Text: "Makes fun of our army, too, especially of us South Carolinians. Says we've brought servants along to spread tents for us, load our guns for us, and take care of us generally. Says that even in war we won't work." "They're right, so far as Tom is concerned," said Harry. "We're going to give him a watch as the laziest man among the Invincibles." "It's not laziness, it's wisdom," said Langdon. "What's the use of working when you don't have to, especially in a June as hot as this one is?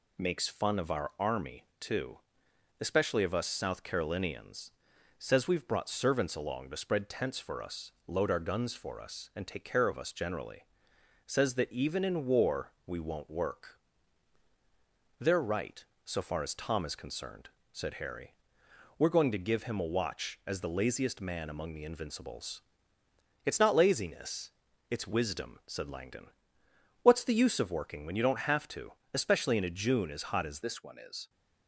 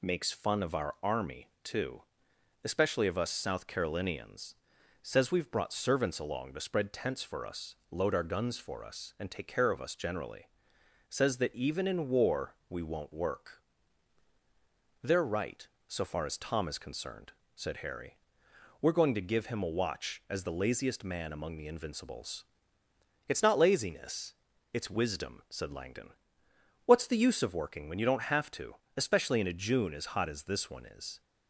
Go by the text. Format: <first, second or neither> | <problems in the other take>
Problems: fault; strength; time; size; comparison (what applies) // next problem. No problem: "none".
second | changes voice at "this"; from 30.6 s on; 0.6 s long